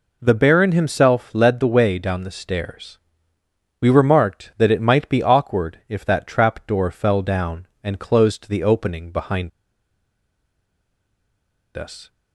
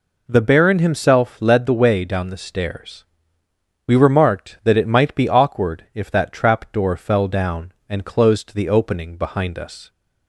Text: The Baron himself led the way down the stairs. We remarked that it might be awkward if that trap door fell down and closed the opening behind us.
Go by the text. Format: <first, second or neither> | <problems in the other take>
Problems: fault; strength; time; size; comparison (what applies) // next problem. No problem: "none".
second | pauses between "behind" and "us"; strong; at 9.5 s; 2.2 s long